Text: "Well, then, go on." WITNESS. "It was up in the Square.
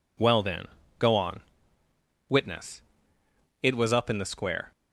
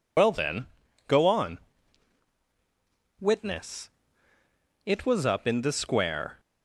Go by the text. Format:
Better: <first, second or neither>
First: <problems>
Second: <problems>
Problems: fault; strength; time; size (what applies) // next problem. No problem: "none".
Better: first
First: none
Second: loses the start of "Well"; at 0.1 s; 85 ms